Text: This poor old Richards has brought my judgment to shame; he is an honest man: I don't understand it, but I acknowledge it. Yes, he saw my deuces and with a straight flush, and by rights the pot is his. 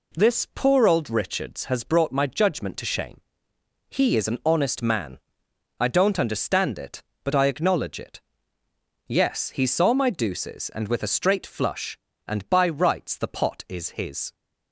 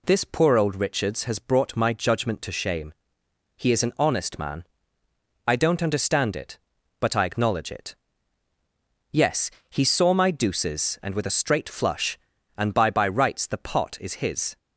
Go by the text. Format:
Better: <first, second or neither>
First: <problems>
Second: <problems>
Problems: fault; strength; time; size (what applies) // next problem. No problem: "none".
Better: first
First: none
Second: says "by" twice; at 12.9 s